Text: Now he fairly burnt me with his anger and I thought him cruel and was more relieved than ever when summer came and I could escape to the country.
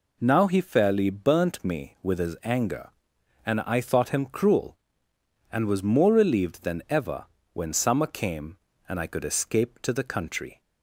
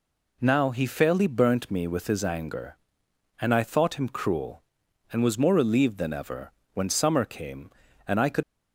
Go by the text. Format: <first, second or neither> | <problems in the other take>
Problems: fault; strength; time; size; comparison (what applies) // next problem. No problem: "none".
first | pauses between "ever" and "when"; slight; at 6.5 s; 0.20 s long; slight in the first // stops before "escape to the country"; at 8.4 s